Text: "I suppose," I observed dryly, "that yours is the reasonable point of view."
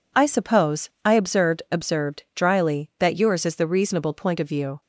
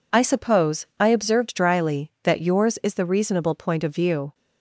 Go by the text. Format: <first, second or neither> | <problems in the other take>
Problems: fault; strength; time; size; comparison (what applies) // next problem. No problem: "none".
second | says "observed" twice; at 1.7 s